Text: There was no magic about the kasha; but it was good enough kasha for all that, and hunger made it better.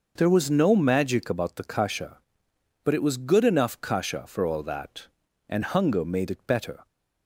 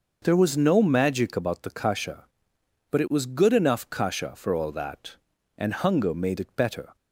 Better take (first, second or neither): neither